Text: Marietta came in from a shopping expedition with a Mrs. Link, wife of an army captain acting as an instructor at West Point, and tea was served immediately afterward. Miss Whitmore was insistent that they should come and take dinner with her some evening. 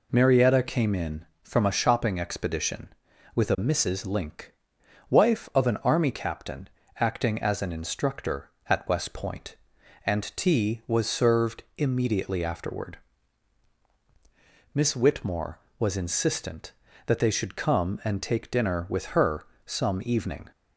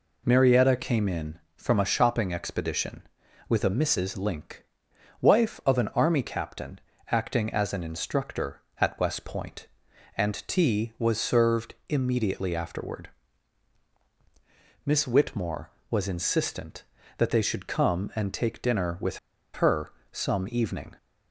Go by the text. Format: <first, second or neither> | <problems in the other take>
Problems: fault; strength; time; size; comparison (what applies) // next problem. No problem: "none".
first | pauses between "captain" and "acting"; slight; at 6.8 s; 0.30 s long; slight in the first // pauses between "served" and "immediately"; slight; at 11.7 s; 0.16 s long; slight in the first // pauses between "with" and "her"; slight; at 19.1 s; 0.35 s long // pauses between "her" and "some"; slight; at 19.9 s; 0.18 s long; slight in the first